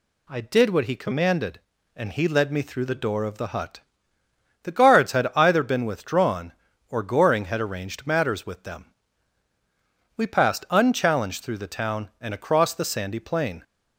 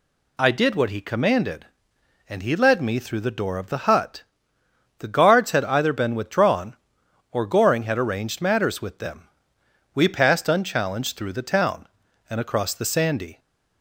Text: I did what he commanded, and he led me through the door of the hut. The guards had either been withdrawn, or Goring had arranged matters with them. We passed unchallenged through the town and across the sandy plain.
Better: first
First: none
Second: stops before "plain"; at 13.3 s

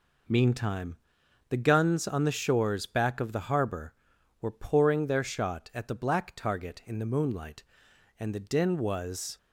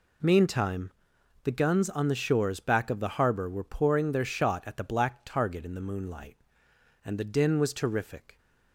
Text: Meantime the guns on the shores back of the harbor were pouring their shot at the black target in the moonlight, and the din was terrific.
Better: second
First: pauses between "Meantime" and "the"; noticeable; at 0.9 s; 0.54 s long // stops before "terrific"; at 9.3 s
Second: pauses between "Meantime" and "the"; noticeable; at 0.9 s; 0.54 s long

